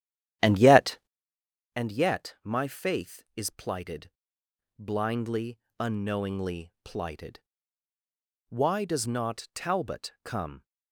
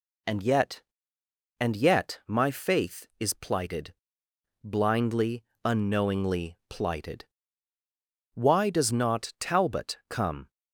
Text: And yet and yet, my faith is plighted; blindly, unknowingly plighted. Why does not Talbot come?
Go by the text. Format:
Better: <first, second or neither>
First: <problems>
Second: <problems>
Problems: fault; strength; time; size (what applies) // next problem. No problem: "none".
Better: second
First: starts louder than the rest; strong; until 1.5 s; 11.5 dB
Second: none